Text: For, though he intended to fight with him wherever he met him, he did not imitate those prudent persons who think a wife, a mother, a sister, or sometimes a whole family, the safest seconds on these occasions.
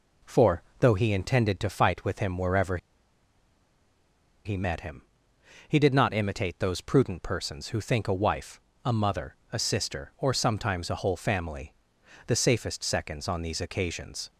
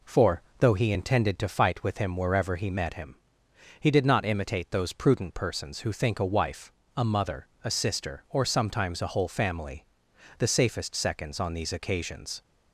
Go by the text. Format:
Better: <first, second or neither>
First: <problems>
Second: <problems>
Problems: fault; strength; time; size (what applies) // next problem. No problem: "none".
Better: second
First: pauses between "wherever" and "he"; strong; at 2.7 s; 1.6 s long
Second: none